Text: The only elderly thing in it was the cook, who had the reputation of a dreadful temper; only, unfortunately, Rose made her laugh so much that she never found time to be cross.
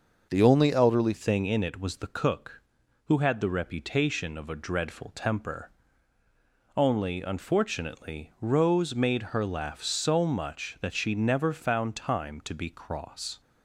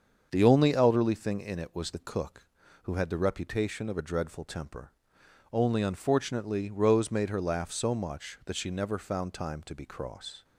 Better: second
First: starts louder than the rest; noticeable; until 1.3 s; 6 dB // changes voice at "thing"; from 1.1 s on; 12.3 s long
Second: starts louder than the rest; until 1.3 s; 7 dB

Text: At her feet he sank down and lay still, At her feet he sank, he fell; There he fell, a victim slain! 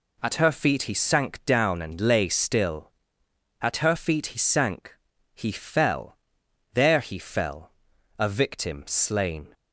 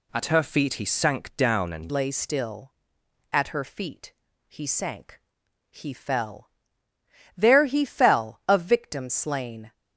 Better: first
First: none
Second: changes voice at "lay"; from 1.9 s on; 7.8 s long // pauses between "feet" and "he"; slight; at 4.1 s; 0.34 s long

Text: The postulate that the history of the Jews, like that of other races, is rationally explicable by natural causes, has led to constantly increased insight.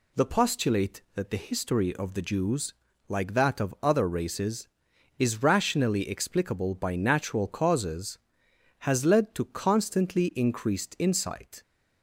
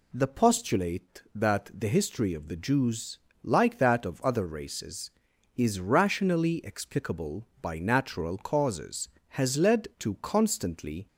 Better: first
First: none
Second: stops before "increased insight"; at 11.0 s

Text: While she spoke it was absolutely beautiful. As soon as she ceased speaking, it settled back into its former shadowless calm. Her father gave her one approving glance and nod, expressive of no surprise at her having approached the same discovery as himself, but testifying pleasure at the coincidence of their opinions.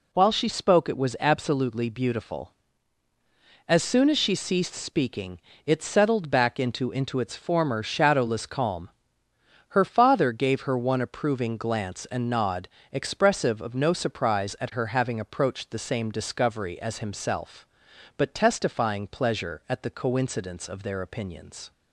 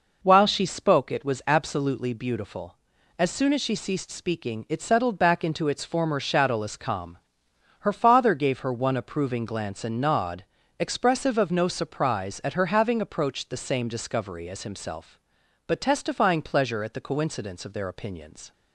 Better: second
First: says "into" twice; at 6.9 s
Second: none

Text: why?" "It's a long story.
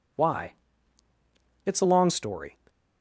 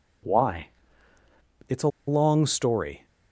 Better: first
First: none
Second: pauses between "a" and "long"; slight; at 1.8 s; 0.19 s long

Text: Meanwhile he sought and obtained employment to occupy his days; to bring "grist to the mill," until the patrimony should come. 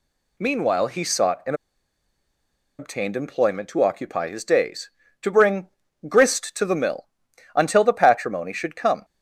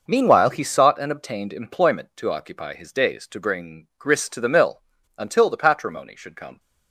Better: second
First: pauses between "and" and "obtained"; at 1.5 s; 1.2 s long // pauses between "bring" and "grist"; at 5.6 s; 0.40 s long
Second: none

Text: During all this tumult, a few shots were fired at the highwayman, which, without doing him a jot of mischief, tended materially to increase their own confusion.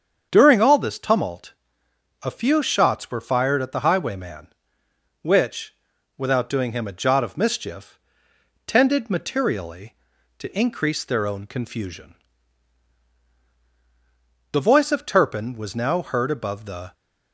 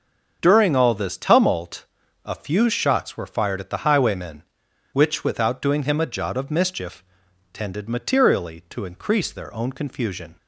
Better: second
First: starts louder than the rest; strong; until 1.3 s; 7.5 dB // goes on to say "The voice of Turpin was now heard above the"; strong; from 14.5 s on; 2.4 s long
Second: starts louder than the rest; until 1.4 s; 6.5 dB

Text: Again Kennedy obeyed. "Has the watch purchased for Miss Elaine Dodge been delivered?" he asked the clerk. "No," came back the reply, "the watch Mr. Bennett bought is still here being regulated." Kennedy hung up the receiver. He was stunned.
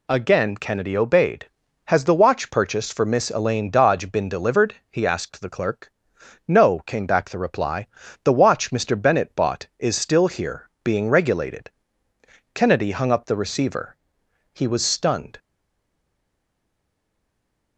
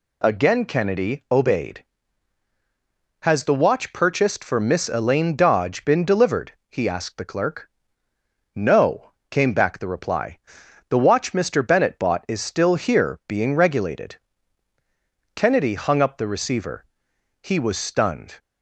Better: second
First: pauses between "here" and "being"; slight; at 10.6 s; 0.16 s long // stays silent after the last word; from 15.3 s on; 2.4 s long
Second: none

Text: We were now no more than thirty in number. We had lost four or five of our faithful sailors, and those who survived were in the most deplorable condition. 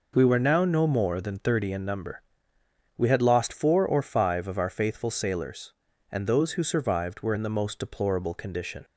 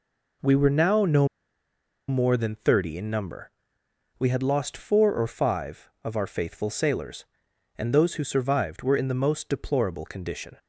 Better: first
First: none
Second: pauses between "no" and "more"; noticeable; at 1.2 s; 0.81 s long

